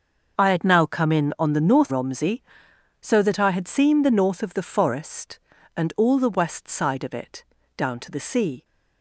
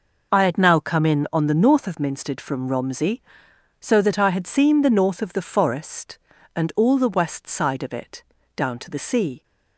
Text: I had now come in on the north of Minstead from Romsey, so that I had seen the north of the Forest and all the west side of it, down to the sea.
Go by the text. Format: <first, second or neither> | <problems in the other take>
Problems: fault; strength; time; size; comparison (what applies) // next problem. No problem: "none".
second | starts louder than the rest; until 1.4 s; 6.5 dB // skips "of Minstead from"; at 1.9 s